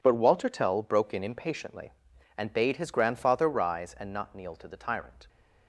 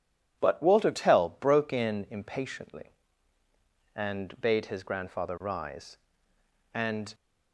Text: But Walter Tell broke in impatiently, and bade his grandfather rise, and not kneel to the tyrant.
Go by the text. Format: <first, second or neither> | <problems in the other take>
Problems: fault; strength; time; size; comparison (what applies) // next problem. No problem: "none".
first | stops before "not kneel to the tyrant"; at 7.1 s